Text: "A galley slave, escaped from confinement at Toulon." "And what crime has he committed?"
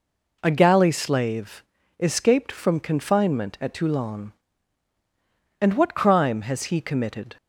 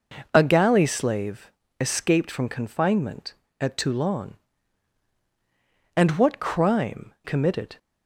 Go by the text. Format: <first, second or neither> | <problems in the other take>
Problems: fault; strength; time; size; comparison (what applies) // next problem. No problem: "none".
first | skips "has he"; at 7.1 s